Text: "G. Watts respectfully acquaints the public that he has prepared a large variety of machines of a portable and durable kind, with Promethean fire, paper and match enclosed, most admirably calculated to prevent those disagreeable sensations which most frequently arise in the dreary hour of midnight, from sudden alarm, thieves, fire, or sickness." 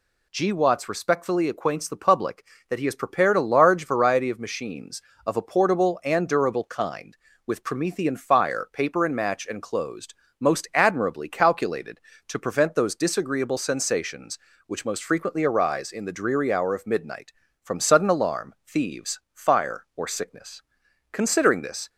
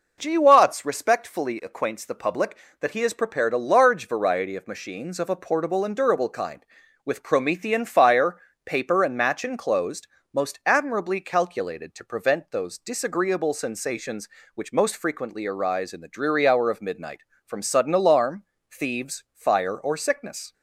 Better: second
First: goes on to say "Considering this"; noticeable; from 21.1 s on; 0.78 s long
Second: none

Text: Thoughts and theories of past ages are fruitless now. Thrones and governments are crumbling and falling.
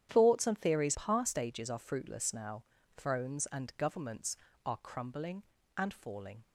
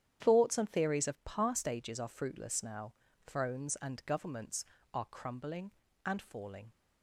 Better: second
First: starts louder than the rest; strong; until 1.1 s; 9.5 dB // skips "of"; at 0.9 s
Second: starts louder than the rest; strong; until 1.2 s; 9.5 dB

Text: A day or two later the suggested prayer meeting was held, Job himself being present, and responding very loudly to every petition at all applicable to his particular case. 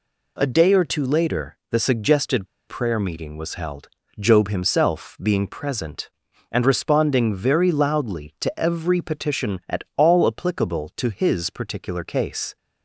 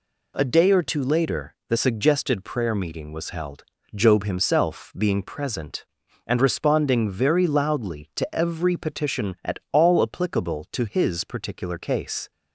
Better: second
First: pauses between "suggested" and "prayer"; slight; at 2.4 s; 0.22 s long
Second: none

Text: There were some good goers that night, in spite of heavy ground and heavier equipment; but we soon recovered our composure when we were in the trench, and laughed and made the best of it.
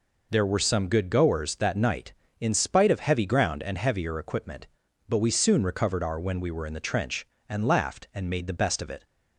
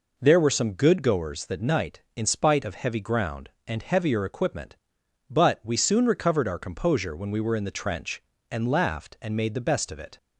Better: second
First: skips "composure"; at 6.1 s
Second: none

